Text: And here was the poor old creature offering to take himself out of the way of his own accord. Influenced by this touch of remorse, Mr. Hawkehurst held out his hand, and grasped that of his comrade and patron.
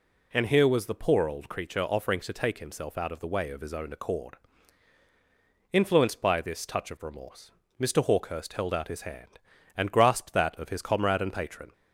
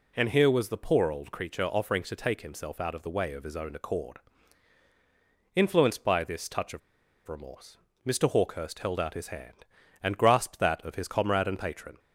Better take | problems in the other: first | pauses between "of" and "remorse"; noticeable; at 6.8 s; 0.48 s long

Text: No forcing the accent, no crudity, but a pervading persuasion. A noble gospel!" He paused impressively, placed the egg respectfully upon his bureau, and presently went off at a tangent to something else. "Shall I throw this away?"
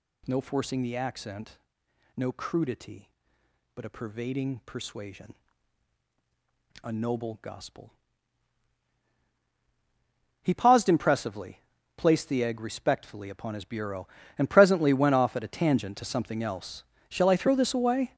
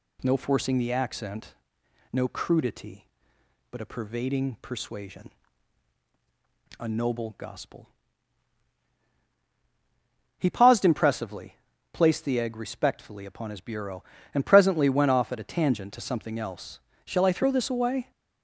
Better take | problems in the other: second | gets louder; strong; throughout; 9 dB

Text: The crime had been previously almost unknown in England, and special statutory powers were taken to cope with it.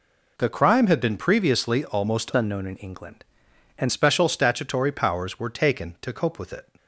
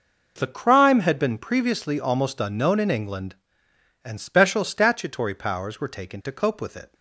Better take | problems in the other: second | changes voice from "unknown" to "and"; from 2.3 to 3.9 s; 1.6 s long

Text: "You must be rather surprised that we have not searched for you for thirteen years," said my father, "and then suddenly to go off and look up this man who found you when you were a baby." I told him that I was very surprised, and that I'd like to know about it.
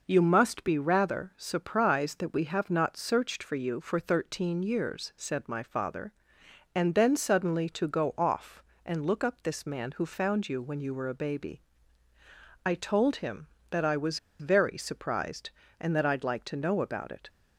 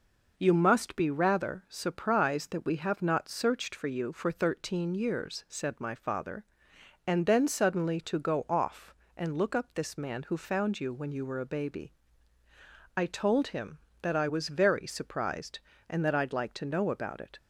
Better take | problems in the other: second | pauses between "was" and "very"; slight; at 14.1 s; 0.21 s long

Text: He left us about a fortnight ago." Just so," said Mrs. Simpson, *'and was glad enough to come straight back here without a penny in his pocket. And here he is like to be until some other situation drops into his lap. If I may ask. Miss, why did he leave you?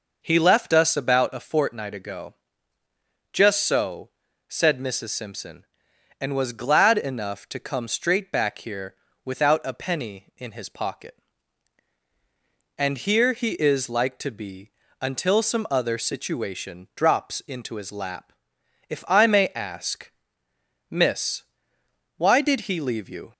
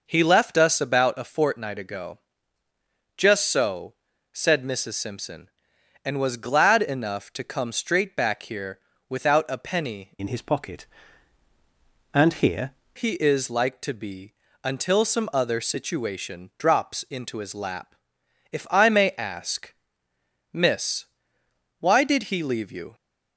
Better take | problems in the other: first | pauses between "here" and "without"; slight; at 8.7 s; 0.30 s long; slight in the first // changes voice from "in" to "here"; from 10.1 to 12.7 s; 2.6 s long // pauses between "be" and "until"; slight; at 14.3 s; 0.30 s long; slight in the first

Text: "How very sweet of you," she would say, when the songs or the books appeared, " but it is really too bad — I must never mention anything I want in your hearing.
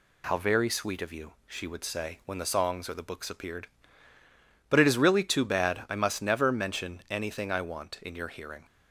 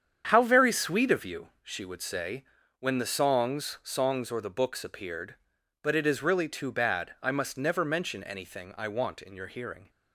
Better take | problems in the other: first | starts louder than the rest; strong; until 1.3 s; 8 dB // says "songs" twice; at 3.8 s

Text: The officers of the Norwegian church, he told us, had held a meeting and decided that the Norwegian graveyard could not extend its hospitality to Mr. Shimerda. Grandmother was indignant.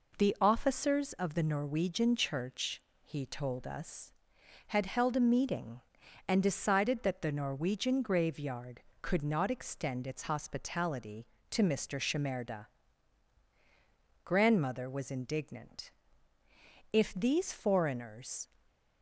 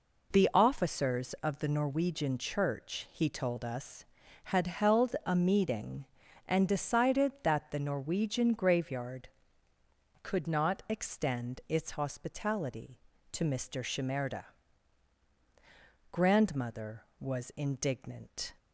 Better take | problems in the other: second | goes on to say "If these foreigners"; from 16.9 s on; 1.5 s long

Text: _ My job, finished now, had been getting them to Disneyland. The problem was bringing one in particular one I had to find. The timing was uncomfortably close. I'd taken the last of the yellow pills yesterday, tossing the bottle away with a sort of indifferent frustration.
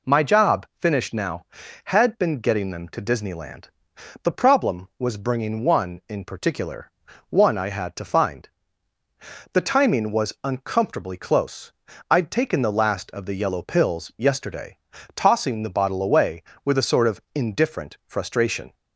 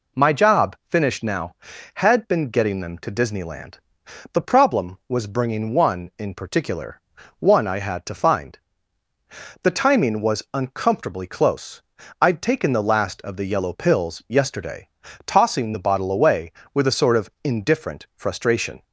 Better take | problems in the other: neither | pauses between "particular" and "one"; the same in both

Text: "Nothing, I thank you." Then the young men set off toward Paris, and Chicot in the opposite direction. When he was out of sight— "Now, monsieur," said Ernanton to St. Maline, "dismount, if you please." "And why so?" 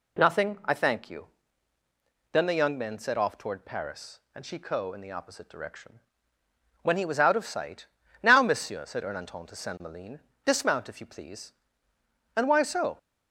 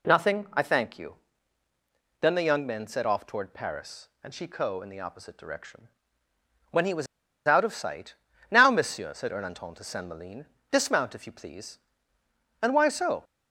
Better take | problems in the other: first | pauses between "was" and "out"; at 7.0 s; 0.41 s long

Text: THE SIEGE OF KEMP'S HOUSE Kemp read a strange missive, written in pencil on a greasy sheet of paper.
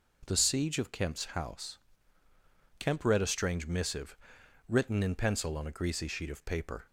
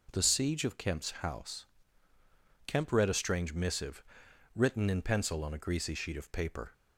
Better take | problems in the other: neither | pauses between "HOUSE" and "Kemp"; the same in both

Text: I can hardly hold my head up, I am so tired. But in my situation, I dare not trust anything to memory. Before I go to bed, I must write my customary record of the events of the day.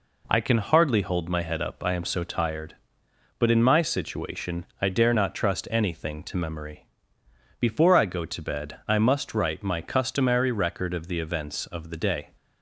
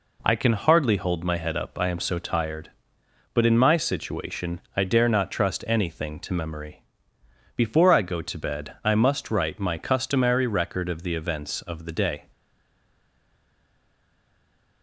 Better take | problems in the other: first | stays silent after the last word; strong; from 12.3 s on; 2.5 s long

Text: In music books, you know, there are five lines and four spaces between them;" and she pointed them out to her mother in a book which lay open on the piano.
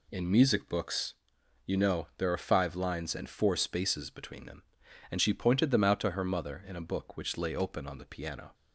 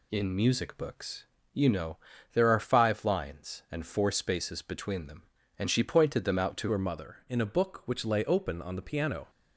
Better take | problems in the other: first | changes voice at "her"; from 6.7 s on; 2.5 s long

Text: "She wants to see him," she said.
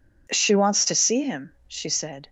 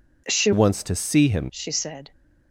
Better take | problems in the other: first | changes voice from "wants" to "him"; from 0.5 to 1.4 s; 0.9 s long

